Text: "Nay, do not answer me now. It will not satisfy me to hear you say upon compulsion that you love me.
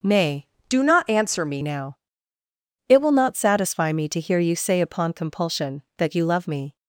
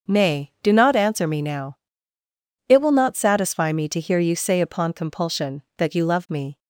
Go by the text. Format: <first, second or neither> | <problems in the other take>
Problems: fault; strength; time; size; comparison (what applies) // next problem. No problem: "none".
second | starts louder than the rest; noticeable; until 1.2 s; 6 dB; also in the second // changes voice from "do" to "me"; from 0.6 to 1.6 s; 1.0 s long